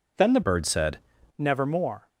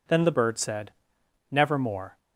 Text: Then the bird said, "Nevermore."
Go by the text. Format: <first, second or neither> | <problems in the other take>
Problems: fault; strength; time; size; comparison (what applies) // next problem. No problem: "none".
second | changes voice from "bird" to "said"; from 0.4 to 0.9 s; 0.5 s long